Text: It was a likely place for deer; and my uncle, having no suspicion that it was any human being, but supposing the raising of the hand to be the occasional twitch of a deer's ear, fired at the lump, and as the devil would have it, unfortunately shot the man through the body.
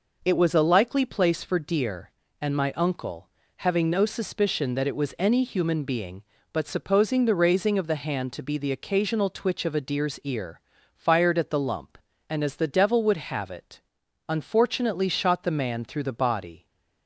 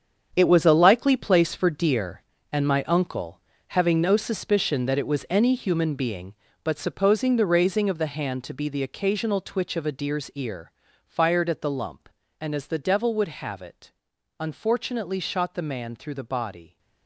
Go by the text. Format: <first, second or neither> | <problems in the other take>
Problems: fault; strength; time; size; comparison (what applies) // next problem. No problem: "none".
first | gets quieter; strong; throughout; 11 dB